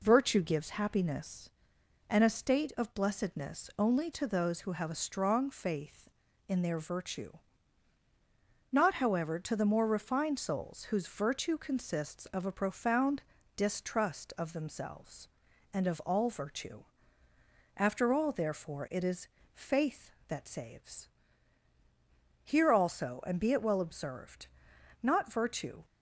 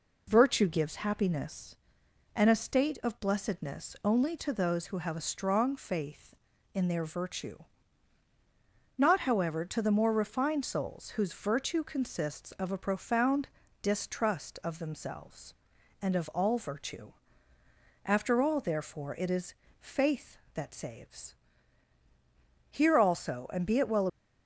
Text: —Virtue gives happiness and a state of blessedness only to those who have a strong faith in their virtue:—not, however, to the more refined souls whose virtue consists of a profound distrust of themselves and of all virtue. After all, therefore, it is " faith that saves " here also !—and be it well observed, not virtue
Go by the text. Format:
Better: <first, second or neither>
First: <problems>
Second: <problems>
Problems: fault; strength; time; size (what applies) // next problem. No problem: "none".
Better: first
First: pauses between "profound" and "distrust"; slight; at 13.2 s; 0.32 s long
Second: pauses between "profound" and "distrust"; slight; at 13.4 s; 0.32 s long // stops before "observed not virtue"; at 24.0 s